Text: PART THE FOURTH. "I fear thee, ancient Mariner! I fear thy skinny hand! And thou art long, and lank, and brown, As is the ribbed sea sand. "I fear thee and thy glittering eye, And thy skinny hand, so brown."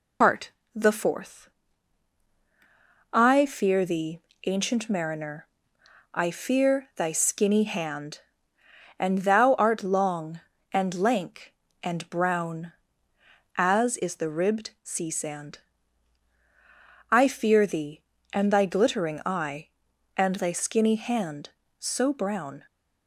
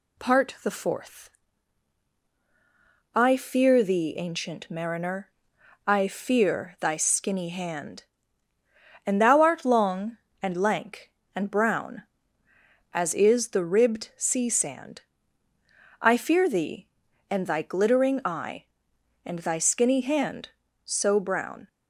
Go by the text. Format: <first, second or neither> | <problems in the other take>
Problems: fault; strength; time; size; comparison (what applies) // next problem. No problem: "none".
second | loses the start of "PART"; at 0.2 s; 95 ms // pauses between "PART" and "THE"; slight; at 0.5 s; 0.24 s long